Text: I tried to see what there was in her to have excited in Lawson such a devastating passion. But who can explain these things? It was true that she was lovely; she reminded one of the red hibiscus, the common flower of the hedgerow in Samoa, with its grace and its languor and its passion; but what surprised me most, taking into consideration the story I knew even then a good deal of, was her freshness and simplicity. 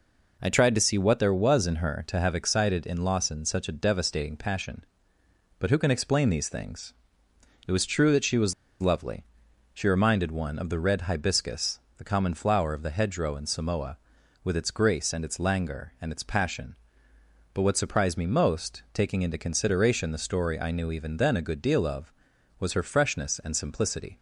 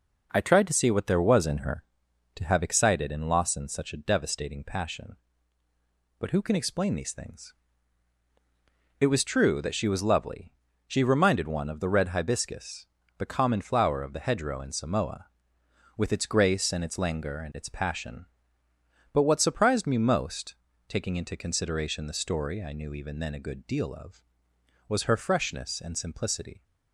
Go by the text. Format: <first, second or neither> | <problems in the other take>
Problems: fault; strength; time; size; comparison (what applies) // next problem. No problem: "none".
second | pauses between "was" and "lovely"; slight; at 8.5 s; 0.27 s long